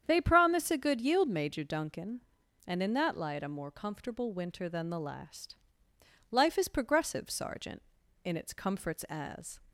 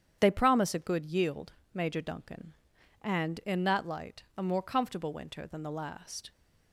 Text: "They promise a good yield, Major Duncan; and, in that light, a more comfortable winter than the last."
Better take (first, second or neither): second